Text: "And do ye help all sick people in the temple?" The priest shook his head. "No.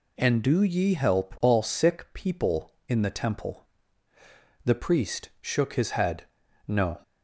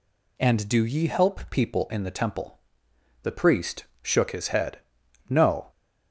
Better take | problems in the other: first | skips "all sick"; at 1.4 s // pauses between "priest" and "shook"; slight; at 3.8 s; 0.18 s long

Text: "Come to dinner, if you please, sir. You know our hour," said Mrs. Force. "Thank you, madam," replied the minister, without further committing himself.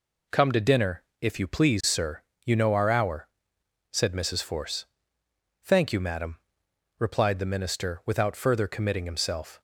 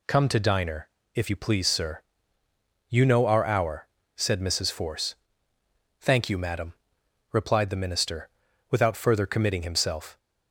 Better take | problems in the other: first | says "diner" for "dinner"; at 0.3 s

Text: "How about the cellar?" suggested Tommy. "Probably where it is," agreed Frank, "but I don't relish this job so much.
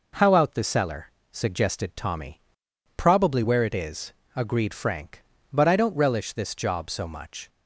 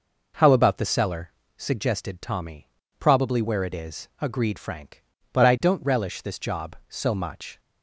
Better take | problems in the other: second | says "out" for "about"; at 0.3 s

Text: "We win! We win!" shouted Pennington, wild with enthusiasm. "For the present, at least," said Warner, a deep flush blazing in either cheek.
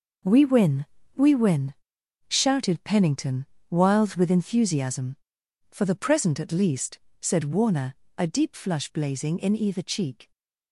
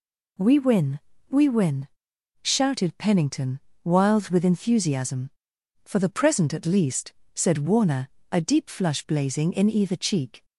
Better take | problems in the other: second | gets quieter; strong; throughout; 11 dB

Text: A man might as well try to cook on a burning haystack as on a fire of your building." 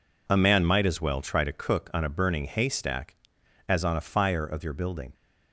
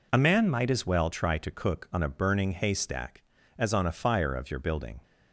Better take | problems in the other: neither | none

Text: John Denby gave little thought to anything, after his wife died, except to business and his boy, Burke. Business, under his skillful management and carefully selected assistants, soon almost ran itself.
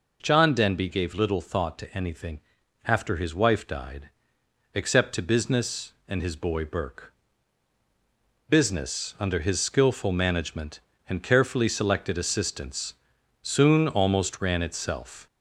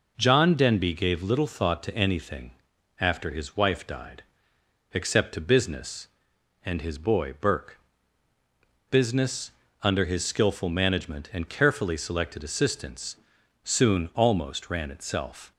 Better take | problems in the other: second | gets louder; slight; throughout; 3 dB

